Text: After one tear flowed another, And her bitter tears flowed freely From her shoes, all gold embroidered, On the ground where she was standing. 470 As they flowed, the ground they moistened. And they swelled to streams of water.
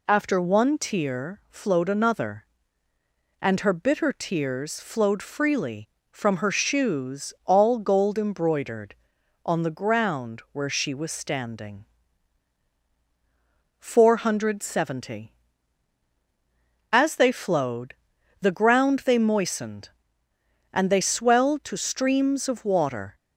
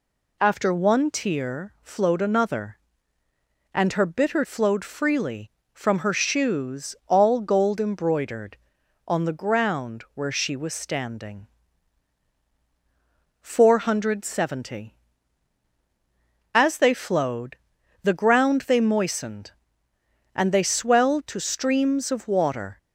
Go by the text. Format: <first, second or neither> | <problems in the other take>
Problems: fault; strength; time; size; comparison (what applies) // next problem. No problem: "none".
first | skips "tears"; at 4.4 s